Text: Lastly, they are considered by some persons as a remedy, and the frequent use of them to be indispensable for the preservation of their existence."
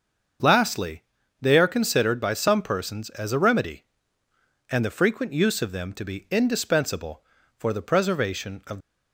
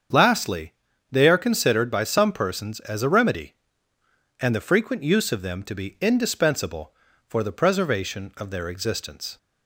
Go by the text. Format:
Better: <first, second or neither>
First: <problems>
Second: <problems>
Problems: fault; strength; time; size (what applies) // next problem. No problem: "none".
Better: second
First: starts louder than the rest; until 1.7 s; 6.5 dB // stops before "their existence"; at 8.7 s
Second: starts louder than the rest; strong; until 1.4 s; 7.5 dB